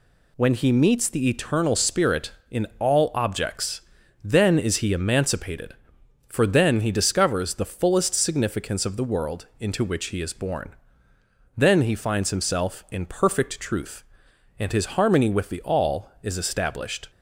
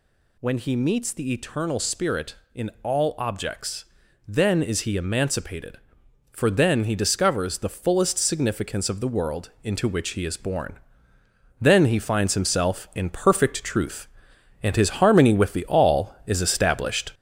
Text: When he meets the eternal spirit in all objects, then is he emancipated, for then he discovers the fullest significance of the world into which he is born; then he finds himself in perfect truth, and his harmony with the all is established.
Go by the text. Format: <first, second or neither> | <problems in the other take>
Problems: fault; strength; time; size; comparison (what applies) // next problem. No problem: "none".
first | gets louder; noticeable; throughout; 5 dB